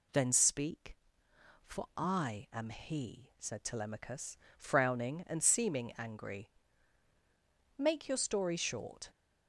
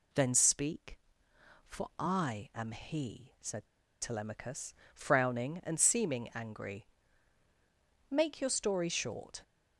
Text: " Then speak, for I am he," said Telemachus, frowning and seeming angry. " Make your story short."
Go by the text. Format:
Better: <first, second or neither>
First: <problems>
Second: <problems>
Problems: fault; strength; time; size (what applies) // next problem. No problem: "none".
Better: first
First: none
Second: pauses between "said" and "Telemachus"; at 3.6 s; 0.36 s long